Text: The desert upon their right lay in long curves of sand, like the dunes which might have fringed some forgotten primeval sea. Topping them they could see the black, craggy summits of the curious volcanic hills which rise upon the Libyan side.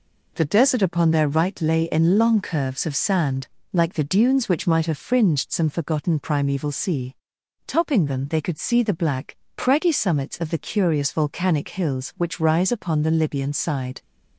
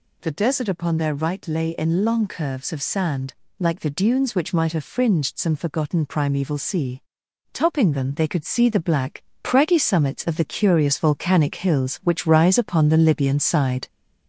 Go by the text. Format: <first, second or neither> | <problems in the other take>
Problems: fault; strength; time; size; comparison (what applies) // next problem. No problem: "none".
first | gets louder; slight; throughout; 3 dB